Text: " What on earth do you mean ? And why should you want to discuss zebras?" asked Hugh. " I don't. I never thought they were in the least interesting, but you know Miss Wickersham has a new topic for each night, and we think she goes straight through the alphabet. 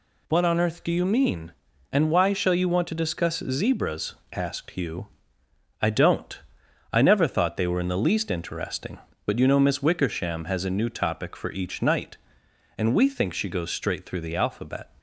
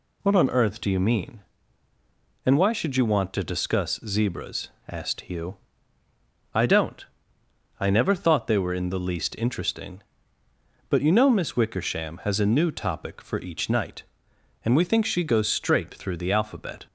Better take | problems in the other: second | says "shall" for "should"; at 2.3 s

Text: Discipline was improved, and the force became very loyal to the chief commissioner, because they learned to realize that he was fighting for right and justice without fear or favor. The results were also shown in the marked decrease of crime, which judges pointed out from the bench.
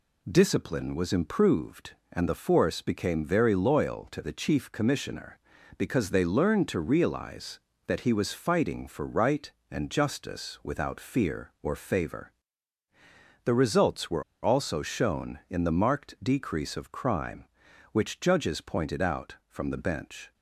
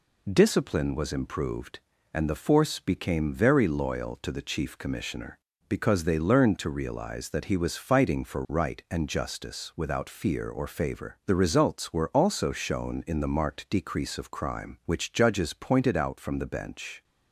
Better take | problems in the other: second | pauses between "were" and "also"; slight; at 14.2 s; 0.20 s long

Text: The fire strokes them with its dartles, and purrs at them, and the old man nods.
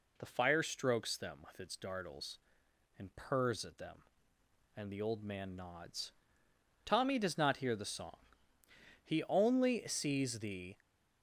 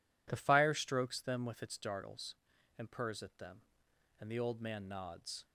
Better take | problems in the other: second | goes on to say "Tommy does not hear the song He only sees the"; strong; from 6.8 s on; 3.9 s long

